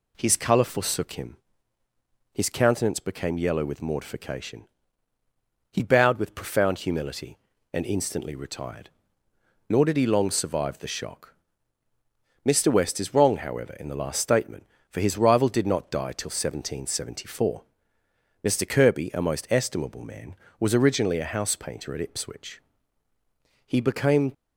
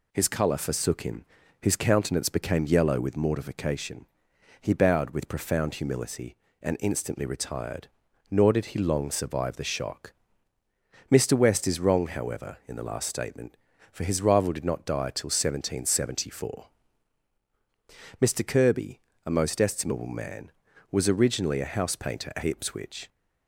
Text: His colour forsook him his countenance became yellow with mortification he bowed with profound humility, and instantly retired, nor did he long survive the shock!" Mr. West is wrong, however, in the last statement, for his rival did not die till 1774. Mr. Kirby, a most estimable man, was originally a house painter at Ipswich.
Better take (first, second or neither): second